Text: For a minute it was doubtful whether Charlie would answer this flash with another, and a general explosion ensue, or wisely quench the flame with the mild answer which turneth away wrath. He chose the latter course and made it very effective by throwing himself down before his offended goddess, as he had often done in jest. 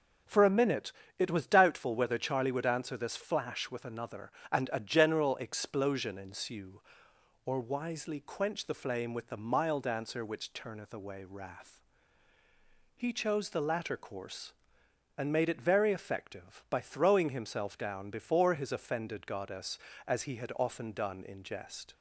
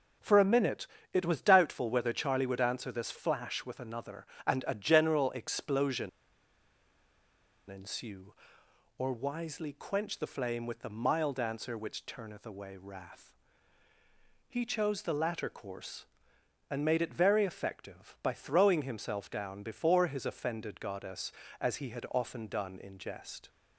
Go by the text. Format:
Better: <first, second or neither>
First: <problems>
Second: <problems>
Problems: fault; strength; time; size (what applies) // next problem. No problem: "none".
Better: first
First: pauses between "minute" and "it"; slight; at 0.9 s; 0.26 s long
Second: pauses between "minute" and "it"; slight; at 0.8 s; 0.26 s long // pauses between "explosion" and "ensue"; strong; at 6.0 s; 1.6 s long